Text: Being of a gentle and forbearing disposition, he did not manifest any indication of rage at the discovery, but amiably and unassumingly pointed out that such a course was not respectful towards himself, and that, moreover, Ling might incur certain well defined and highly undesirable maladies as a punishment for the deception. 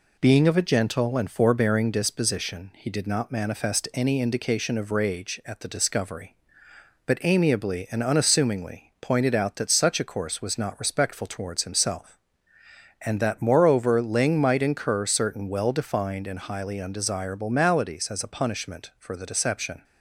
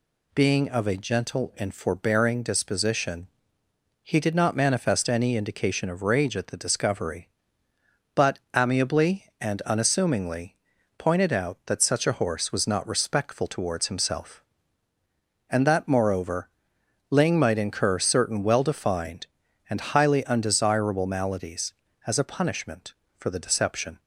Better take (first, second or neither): first